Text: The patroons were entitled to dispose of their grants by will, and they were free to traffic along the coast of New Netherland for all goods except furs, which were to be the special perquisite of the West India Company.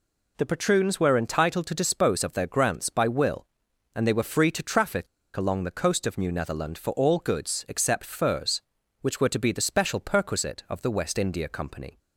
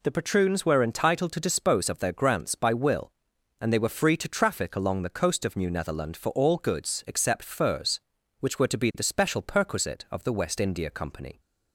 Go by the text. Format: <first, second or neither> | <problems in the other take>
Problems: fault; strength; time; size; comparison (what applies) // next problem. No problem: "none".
second | pauses between "traffic" and "along"; slight; at 5.0 s; 0.29 s long